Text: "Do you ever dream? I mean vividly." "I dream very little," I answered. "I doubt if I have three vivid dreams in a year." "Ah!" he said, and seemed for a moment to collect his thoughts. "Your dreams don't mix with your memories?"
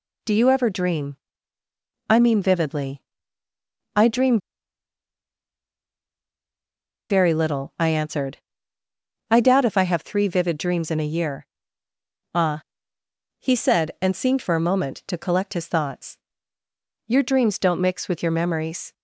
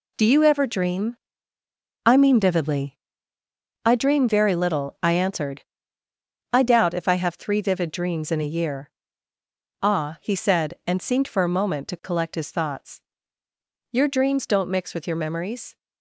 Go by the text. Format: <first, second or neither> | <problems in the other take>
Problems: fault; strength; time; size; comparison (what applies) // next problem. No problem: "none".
second | pauses between "dream" and "very"; strong; at 4.3 s; 2.7 s long